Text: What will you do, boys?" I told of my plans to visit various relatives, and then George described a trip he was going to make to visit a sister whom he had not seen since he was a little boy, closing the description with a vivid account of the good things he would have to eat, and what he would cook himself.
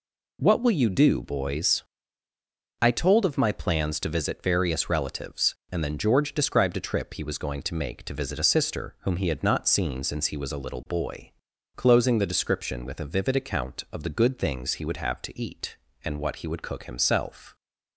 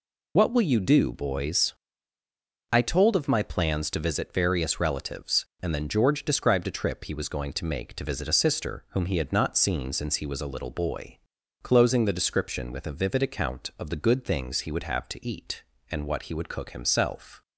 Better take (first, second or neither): first